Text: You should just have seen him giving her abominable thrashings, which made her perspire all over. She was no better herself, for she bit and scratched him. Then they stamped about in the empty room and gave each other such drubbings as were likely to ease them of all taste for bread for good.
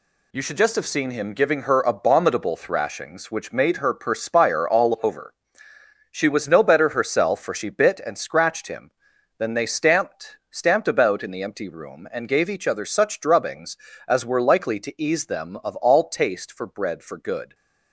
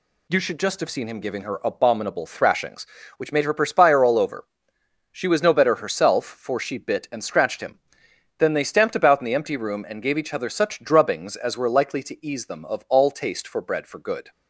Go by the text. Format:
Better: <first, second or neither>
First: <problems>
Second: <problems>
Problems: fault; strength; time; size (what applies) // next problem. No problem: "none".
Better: second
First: says "stamped" twice; at 10.5 s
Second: none